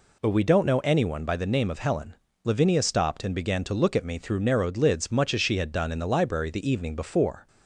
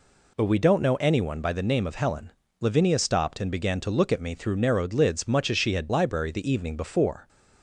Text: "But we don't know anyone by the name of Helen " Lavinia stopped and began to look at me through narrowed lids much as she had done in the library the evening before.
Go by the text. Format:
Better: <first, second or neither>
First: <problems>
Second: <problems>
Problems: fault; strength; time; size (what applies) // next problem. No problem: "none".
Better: first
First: none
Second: skips "done in the"; at 5.8 s